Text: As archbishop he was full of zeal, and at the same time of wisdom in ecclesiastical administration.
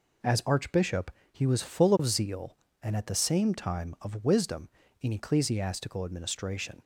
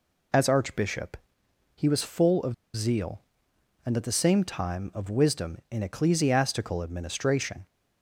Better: first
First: pauses between "archbishop" and "he"; slight; at 1.0 s; 0.22 s long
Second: pauses between "archbishop" and "he"; noticeable; at 1.1 s; 0.58 s long // pauses between "of" and "zeal"; slight; at 2.5 s; 0.20 s long

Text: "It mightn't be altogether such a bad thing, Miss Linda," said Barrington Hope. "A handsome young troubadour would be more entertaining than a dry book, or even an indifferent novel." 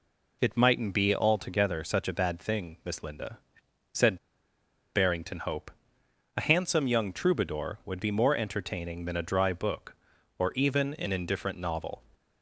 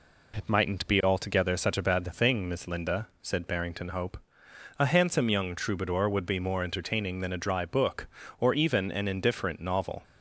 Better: second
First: pauses between "said" and "Barrington"; noticeable; at 4.1 s; 0.78 s long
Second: none

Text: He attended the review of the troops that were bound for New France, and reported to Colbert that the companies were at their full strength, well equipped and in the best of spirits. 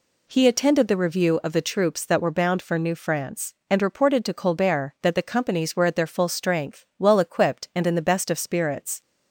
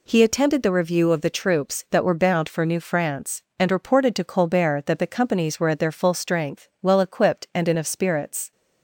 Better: first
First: none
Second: skips "the best"; at 7.7 s

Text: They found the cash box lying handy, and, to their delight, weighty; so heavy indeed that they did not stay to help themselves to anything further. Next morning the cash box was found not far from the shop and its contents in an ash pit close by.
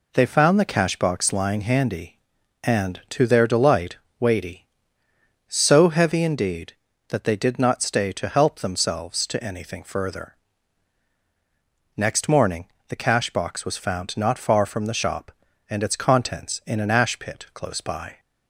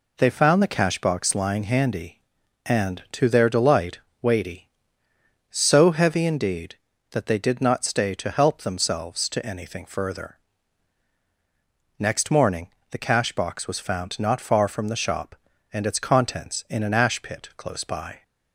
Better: neither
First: pauses between "morning" and "the"; slight; at 12.6 s; 0.22 s long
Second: pauses between "morning" and "the"; slight; at 12.6 s; 0.22 s long

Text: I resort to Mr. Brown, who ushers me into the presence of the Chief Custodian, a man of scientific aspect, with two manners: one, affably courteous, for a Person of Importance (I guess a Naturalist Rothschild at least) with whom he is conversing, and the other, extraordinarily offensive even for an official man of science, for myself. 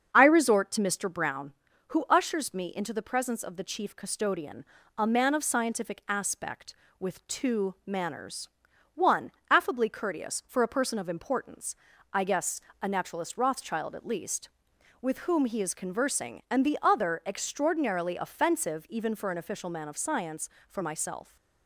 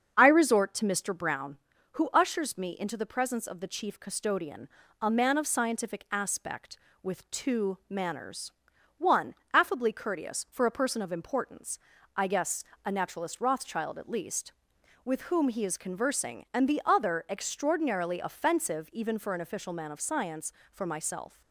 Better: neither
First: starts louder than the rest; until 1.1 s; 7 dB // pauses between "guess" and "a"; slight; at 12.6 s; 0.20 s long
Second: starts louder than the rest; until 1.1 s; 7 dB // pauses between "guess" and "a"; slight; at 12.6 s; 0.20 s long

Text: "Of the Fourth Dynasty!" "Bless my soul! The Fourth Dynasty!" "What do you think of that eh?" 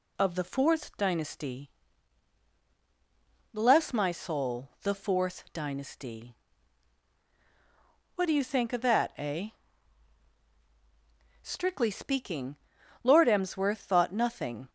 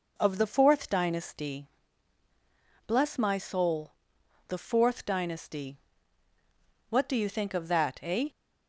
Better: second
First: goes on to say "Strictly speaking Lord Emsworth thought nothing"; strong; from 11.4 s on; 3.2 s long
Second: none

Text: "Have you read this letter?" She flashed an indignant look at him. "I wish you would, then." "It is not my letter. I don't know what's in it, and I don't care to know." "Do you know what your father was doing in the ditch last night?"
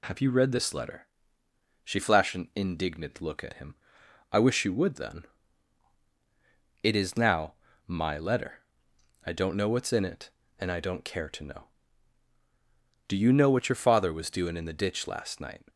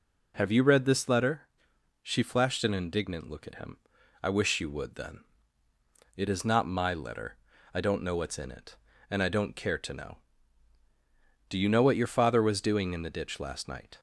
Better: second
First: says "now" for "not"; at 7.1 s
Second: none

